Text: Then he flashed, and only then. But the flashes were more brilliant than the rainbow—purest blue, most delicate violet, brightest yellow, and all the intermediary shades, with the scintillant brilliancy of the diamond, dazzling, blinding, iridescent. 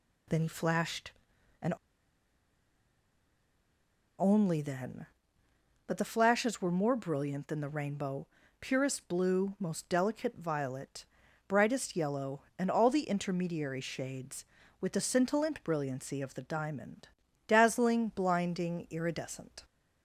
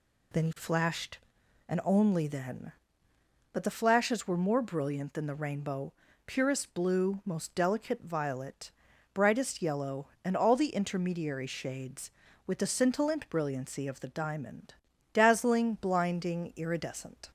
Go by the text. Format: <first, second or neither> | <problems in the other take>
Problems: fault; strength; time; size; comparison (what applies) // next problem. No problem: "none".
second | pauses between "and" and "only"; strong; at 1.7 s; 2.4 s long